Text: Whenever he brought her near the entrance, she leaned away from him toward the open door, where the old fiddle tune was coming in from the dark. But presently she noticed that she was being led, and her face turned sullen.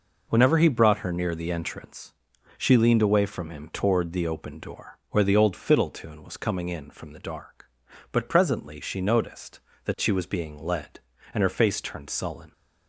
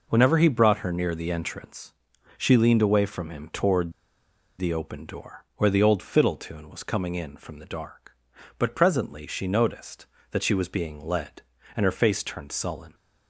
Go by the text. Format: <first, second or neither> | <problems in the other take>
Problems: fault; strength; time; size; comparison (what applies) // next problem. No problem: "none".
first | pauses between "toward" and "the"; noticeable; at 3.9 s; 0.66 s long